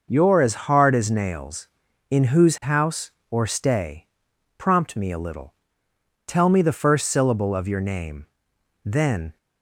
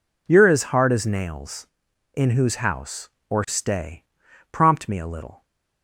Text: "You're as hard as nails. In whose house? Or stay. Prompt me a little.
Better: second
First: goes on to say "Tell me the first syllable of your name Then"; strong; from 6.2 s on; 3.1 s long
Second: none

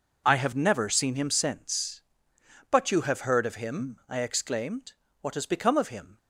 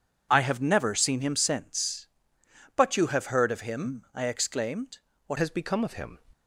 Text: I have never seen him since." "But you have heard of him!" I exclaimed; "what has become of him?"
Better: first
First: none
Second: changes voice at "has"; from 5.3 s on; 0.8 s long

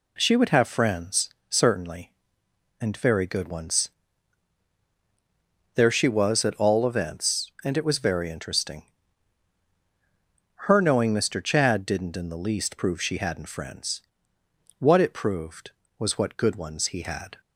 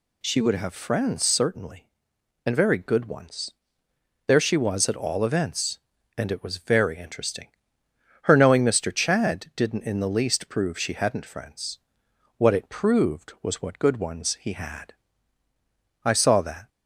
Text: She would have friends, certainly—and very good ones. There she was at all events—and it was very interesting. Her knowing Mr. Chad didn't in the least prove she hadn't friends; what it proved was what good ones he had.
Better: first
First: none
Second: goes on to say "I saw that"; noticeable; from 16.0 s on; 0.64 s long

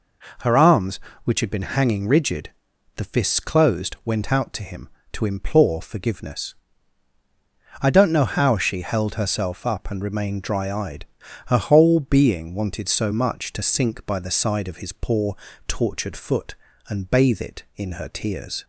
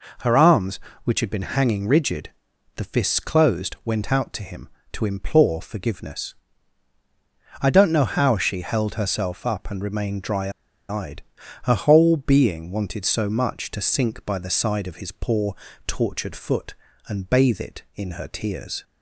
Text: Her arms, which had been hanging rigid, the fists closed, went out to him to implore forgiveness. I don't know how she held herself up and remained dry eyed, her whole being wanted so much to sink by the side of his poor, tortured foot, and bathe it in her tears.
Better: first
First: none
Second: pauses between "dry" and "eyed"; at 10.5 s; 0.38 s long

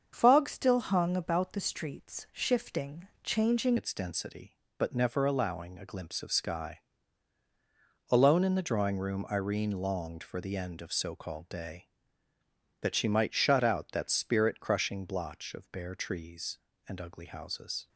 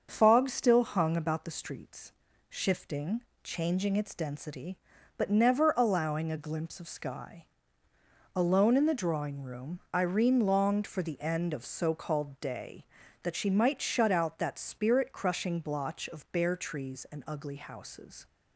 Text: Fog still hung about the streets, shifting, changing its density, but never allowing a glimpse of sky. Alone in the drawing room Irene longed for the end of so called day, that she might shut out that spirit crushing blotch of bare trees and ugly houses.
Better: second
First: starts louder than the rest; until 1.1 s; 7 dB // changes voice at "its"; from 3.7 s on; 14.1 s long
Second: starts louder than the rest; until 1.1 s; 6.5 dB

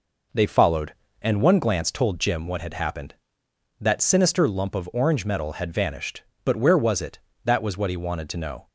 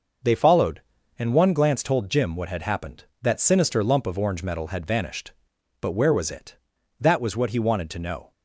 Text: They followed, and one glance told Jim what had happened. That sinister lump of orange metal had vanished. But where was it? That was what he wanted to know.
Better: neither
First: none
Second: none

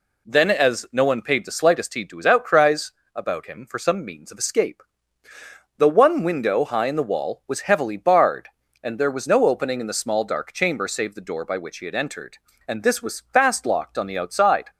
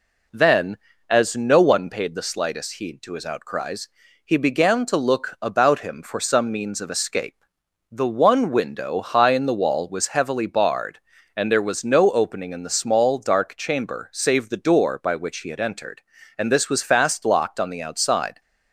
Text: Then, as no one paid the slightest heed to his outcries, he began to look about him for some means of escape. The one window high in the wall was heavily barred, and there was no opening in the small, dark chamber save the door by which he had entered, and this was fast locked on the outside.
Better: second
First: skips "he began to look"; at 3.0 s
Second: none

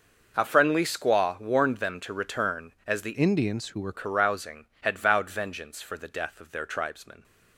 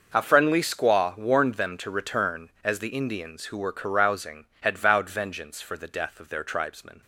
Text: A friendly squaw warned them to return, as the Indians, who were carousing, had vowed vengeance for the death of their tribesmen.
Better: second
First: changes voice from "Indians" to "were"; from 3.1 to 3.9 s; 0.8 s long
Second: none

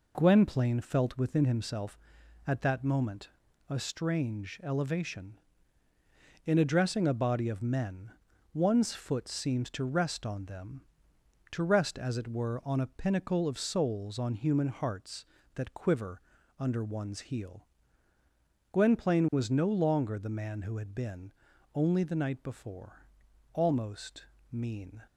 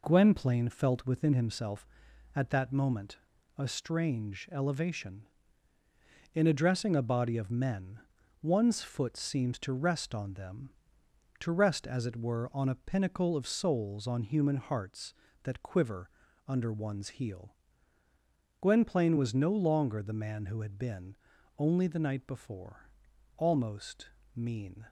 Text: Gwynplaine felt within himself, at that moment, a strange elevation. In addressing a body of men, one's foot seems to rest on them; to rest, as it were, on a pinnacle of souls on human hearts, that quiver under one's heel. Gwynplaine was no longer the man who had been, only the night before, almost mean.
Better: neither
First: pauses between "quiver" and "under"; slight; at 16.2 s; 0.36 s long // pauses between "almost" and "mean"; slight; at 24.2 s; 0.26 s long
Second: pauses between "quiver" and "under"; slight; at 16.1 s; 0.36 s long // pauses between "almost" and "mean"; slight; at 24.0 s; 0.26 s long

